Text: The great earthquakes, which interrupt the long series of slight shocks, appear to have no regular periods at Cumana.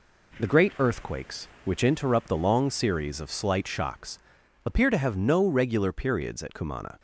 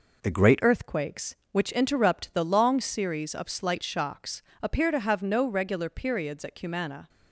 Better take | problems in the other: first | changes voice at "earthquakes"; from 0.6 s on; 6.4 s long

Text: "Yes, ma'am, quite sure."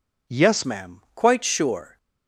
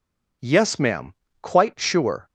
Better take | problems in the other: second | changes voice at "ma'am"; from 0.6 s on; 1.3 s long

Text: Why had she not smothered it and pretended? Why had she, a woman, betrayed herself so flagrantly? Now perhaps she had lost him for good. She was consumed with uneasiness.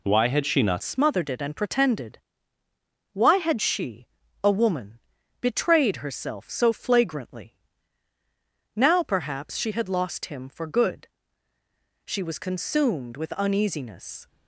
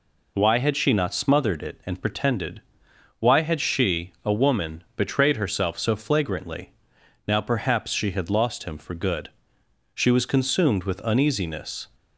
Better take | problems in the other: second | changes voice at "smothered"; from 0.8 s on; 13.4 s long

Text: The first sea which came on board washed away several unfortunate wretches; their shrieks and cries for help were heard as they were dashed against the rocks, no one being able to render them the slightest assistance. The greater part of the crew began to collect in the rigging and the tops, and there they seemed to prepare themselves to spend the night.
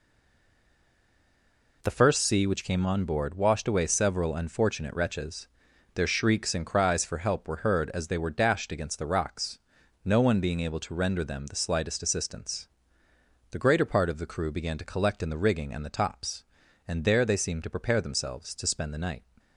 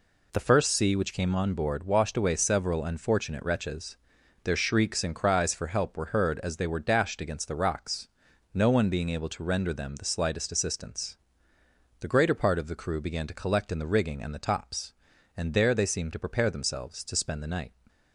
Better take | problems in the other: second | stays silent before the first word; noticeable; until 1.8 s; 1.8 s long

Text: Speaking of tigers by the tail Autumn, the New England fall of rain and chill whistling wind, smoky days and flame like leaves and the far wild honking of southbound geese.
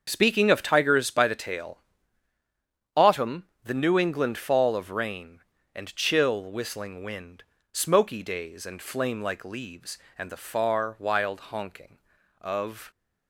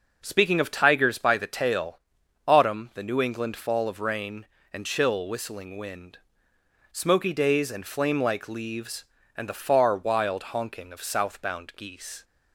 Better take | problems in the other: second | starts louder than the rest; until 1.0 s; 7 dB // pauses between "tail" and "Autumn"; at 1.8 s; 1.1 s long; noticeable in the second // stops before "southbound geese"; at 12.9 s

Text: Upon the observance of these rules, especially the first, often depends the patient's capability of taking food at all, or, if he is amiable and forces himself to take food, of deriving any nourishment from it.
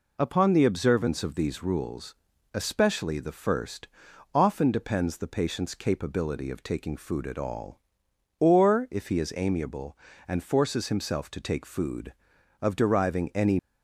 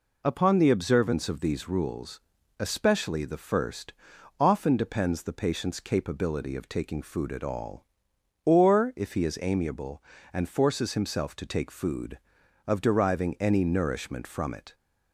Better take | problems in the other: second | stops before "nourishment from it"; at 13.5 s

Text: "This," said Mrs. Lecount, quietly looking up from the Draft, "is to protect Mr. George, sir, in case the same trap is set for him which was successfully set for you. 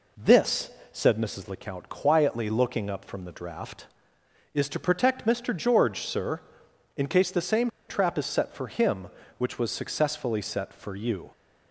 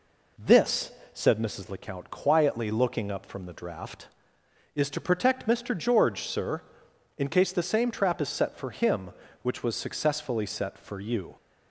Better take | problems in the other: second | pauses between "same" and "trap"; slight; at 7.6 s; 0.19 s long

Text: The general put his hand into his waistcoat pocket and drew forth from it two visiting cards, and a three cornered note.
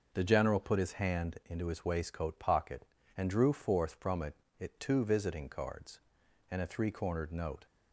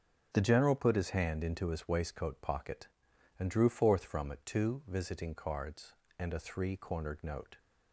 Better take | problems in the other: second | starts louder than the rest; noticeable; until 1.1 s; 6 dB; also in the second // says "it" twice; at 4.5 s

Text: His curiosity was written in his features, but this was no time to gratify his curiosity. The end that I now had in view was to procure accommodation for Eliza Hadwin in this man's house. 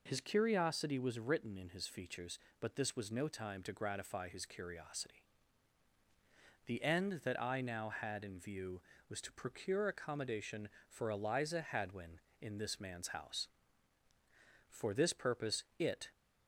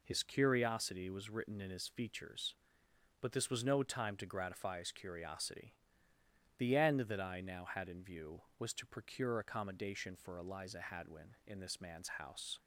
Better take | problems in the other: second | goes on to say "For this purpose it"; from 14.7 s on; 1.4 s long

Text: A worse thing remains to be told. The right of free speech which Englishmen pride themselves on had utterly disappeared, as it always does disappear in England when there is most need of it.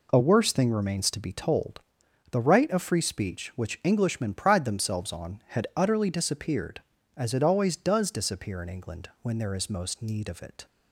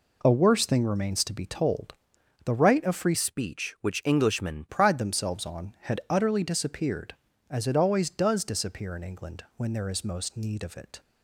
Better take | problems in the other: first | changes voice from "speech" to "Englishmen"; from 3.1 to 4.6 s; 1.5 s long

